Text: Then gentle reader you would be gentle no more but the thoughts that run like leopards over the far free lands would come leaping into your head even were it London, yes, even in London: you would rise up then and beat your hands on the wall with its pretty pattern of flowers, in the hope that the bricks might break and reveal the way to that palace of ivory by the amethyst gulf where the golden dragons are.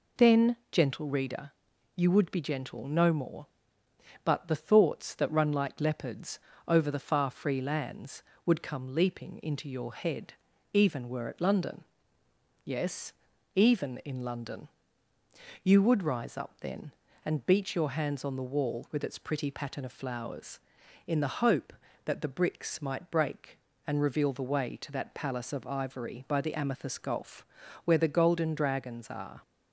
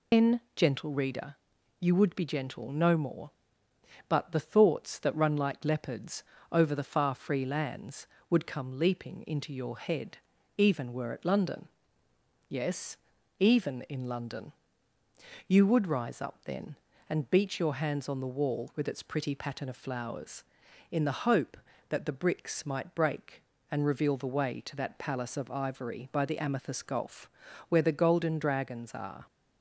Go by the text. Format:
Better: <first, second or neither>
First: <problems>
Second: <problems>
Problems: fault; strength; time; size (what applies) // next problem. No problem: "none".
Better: first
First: pauses between "Then" and "gentle"; slight; at 0.5 s; 0.16 s long // pauses between "reader" and "you"; at 1.5 s; 0.44 s long // pauses between "leopards" and "over"; slight; at 6.3 s; 0.28 s long // pauses between "head" and "even"; at 10.3 s; 0.40 s long // pauses between "gulf" and "where"; at 27.4 s; 0.40 s long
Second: loses the start of "Then"; at 0.1 s; 100 ms // pauses between "Then" and "gentle"; slight; at 0.4 s; 0.16 s long // pauses between "reader" and "you"; at 1.3 s; 0.44 s long // pauses between "leopards" and "over"; slight; at 6.2 s; 0.28 s long // pauses between "head" and "even"; at 10.1 s; 0.40 s long // pauses between "gulf" and "where"; at 27.2 s; 0.40 s long